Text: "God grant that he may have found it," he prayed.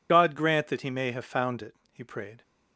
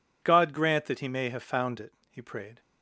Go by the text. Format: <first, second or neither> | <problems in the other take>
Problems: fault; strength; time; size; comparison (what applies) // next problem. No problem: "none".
second | loses the start of "God"; at 0.0 s; 35 ms